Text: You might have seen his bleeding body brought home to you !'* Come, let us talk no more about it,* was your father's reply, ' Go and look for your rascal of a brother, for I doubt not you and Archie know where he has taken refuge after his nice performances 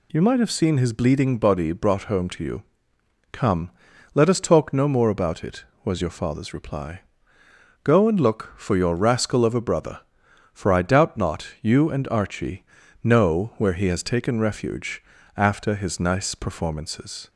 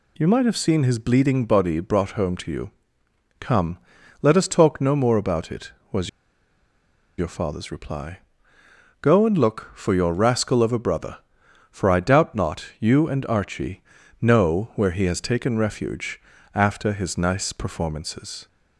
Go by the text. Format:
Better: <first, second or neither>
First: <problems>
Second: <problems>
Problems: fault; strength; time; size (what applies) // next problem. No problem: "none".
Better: first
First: pauses between "Archie" and "know"; at 12.6 s; 0.40 s long // pauses between "refuge" and "after"; slight; at 15.0 s; 0.32 s long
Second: pauses between "was" and "your"; at 6.0 s; 1.0 s long // pauses between "Archie" and "know"; at 13.8 s; 0.40 s long // pauses between "refuge" and "after"; slight; at 16.2 s; 0.32 s long